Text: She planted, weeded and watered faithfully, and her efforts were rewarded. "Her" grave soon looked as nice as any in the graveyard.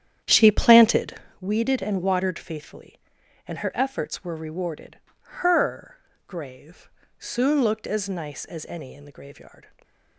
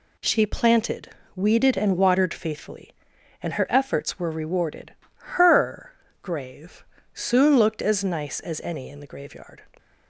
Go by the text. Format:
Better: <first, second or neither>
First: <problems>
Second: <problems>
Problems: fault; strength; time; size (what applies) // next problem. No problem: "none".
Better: second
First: starts louder than the rest; strong; until 1.4 s; 9.5 dB // pauses between "Her" and "grave"; slight; at 5.9 s; 0.32 s long // pauses between "grave" and "soon"; slight; at 6.8 s; 0.30 s long // stays silent after the last word; slight; from 9.6 s on; 0.5 s long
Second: pauses between "Her" and "grave"; slight; at 5.9 s; 0.32 s long // pauses between "grave" and "soon"; slight; at 6.8 s; 0.30 s long